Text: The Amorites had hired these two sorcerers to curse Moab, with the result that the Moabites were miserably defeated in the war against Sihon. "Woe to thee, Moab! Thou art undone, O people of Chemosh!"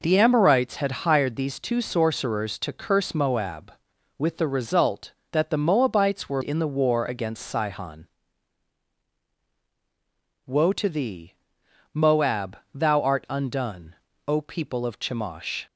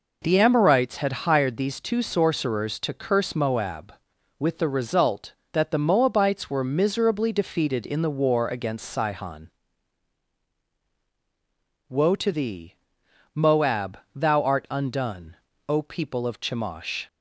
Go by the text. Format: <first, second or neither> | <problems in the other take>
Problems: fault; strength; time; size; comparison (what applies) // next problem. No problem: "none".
second | skips "miserably defeated"; at 6.4 s